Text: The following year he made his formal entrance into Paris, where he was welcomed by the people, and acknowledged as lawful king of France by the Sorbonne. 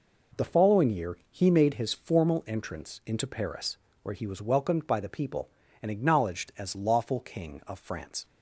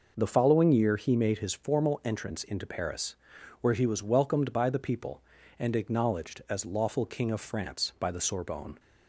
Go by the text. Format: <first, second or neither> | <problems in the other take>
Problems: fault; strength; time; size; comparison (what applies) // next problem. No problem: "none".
second | stops before "by the Sorbonne"; at 8.2 s